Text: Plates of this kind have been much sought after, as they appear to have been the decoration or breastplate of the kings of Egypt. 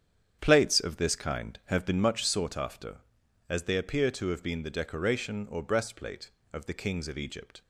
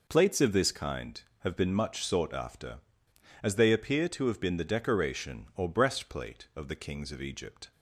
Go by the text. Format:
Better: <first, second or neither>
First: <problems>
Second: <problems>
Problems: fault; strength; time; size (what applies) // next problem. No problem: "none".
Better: second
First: starts louder than the rest; strong; until 2.3 s; 8.5 dB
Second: none